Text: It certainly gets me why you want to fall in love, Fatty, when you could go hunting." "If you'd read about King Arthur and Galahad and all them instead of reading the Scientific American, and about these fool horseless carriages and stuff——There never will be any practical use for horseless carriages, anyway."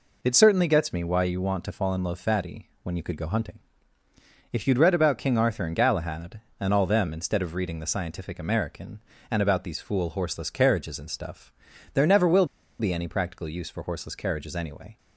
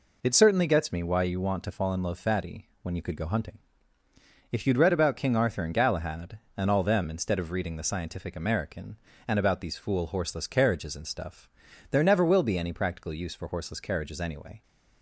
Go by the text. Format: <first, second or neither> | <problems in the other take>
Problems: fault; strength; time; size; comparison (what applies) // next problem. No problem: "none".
second | pauses between "will" and "be"; slight; at 12.4 s; 0.34 s long